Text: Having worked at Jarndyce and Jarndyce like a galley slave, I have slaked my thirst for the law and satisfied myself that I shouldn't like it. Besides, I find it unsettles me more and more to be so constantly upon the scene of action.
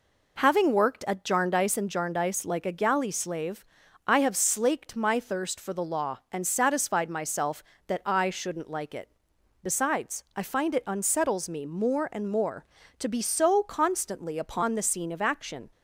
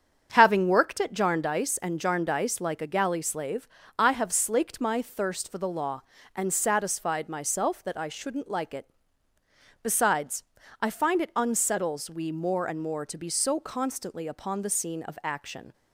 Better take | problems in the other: first | starts louder than the rest; strong; until 1.3 s; 8 dB // says "we" for "me"; at 12.0 s

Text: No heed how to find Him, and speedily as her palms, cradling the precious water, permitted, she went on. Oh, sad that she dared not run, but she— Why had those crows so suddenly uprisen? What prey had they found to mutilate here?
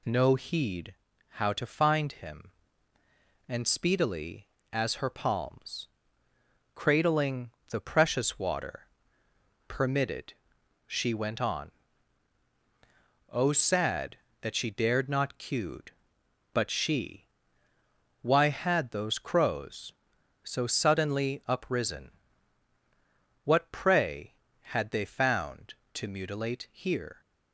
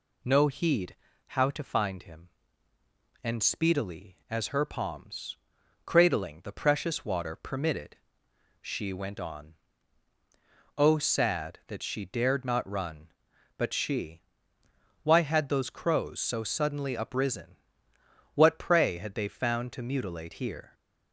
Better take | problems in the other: second | pauses between "heed" and "how"; slight; at 0.9 s; 0.36 s long; slight in the second // pauses between "cradling" and "the"; slight; at 7.4 s; 0.20 s long // says "cued" for "run"; at 15.3 s

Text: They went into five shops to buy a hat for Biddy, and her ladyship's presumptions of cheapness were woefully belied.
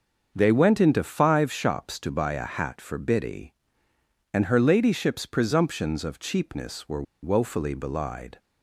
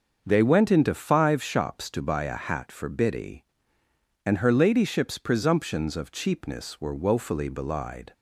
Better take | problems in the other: second | starts louder than the rest; until 1.3 s; 6.5 dB; also in the second // pauses between "were" and "woefully"; slight; at 7.0 s; 0.20 s long

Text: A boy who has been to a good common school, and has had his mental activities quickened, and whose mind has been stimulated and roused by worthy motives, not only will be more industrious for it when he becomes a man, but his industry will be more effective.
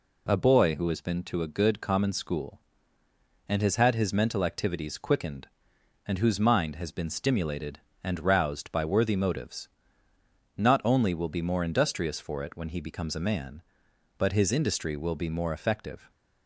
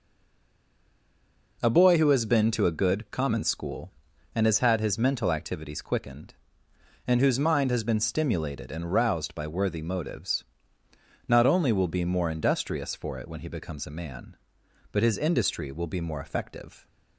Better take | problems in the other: first | stays silent before the first word; noticeable; until 1.5 s; 1.5 s long

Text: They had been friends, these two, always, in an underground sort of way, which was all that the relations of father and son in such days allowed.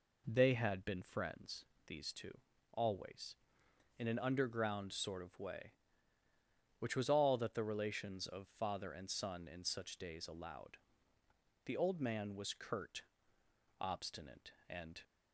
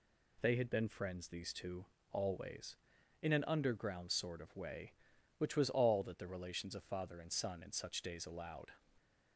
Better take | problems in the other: second | goes on to say "The old man was curt obstinate and"; strong; from 11.6 s on; 3.3 s long

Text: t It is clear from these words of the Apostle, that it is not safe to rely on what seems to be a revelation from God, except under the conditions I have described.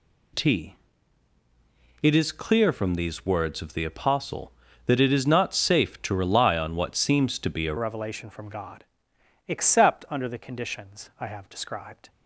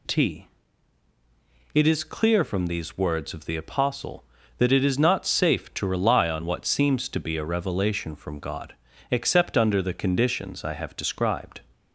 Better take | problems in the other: second | pauses between "t" and "It"; strong; at 0.7 s; 1.2 s long; strong in the second // changes voice at "revelation"; from 7.7 s on; 4.3 s long

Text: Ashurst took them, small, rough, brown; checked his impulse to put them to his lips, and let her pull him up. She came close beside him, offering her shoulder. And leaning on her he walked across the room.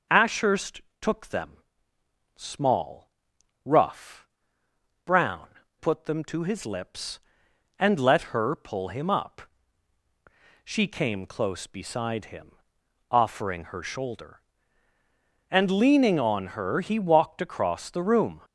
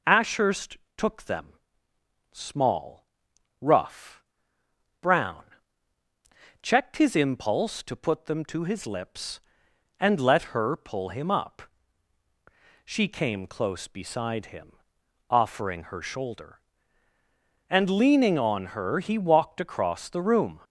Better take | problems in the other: second | starts louder than the rest; noticeable; until 1.3 s; 6 dB // pauses between "Ashurst" and "took"; slight; at 0.8 s; 0.22 s long; slight in the second // skips "checked his impulse to"; at 5.6 s

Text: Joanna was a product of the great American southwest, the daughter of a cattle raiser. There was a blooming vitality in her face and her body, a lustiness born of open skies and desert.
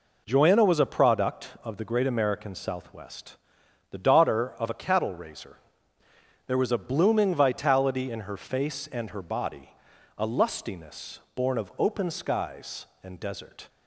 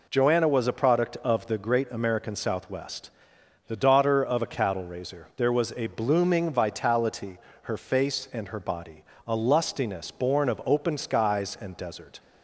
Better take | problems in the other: first | skips "in"; at 7.5 s

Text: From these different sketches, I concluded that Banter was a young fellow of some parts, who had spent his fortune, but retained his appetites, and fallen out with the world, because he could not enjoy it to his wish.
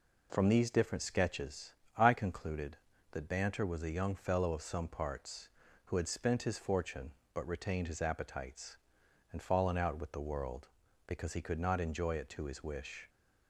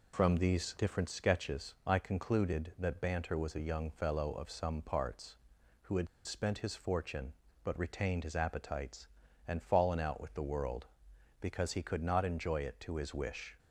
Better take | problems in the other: first | pauses between "had" and "spent"; slight; at 6.0 s; 0.19 s long

